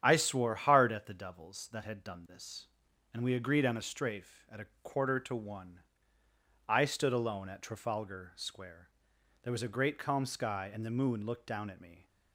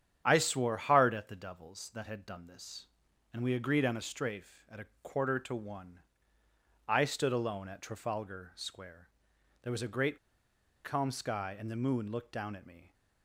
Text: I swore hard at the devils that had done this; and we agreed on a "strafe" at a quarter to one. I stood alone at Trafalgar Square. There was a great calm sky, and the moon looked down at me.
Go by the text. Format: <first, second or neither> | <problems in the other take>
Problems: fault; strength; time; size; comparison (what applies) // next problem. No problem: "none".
first | starts louder than the rest; strong; until 1.2 s; 9 dB; strong in the first // pauses between "a" and "quarter"; slight; at 4.8 s; 0.18 s long; slight in the first // pauses between "great" and "calm"; noticeable; at 10.1 s; 0.67 s long